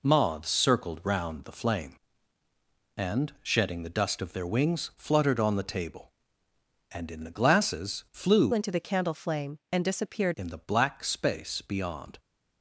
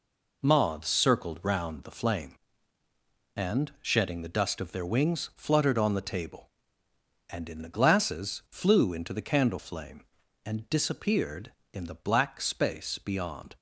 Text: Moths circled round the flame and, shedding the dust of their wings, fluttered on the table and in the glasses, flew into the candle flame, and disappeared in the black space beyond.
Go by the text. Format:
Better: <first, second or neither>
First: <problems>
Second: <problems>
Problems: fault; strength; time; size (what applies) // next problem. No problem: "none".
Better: second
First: changes voice from "into" to "disappeared"; from 8.5 to 10.3 s; 1.8 s long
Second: none